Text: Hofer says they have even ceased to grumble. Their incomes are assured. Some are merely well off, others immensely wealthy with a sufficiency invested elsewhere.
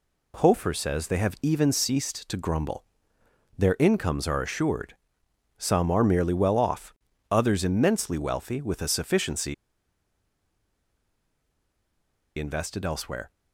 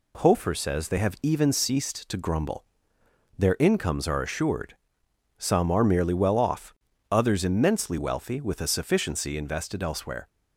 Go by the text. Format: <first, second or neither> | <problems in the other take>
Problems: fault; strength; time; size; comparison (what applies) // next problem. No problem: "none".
second | pauses between "sufficiency" and "invested"; strong; at 9.5 s; 2.8 s long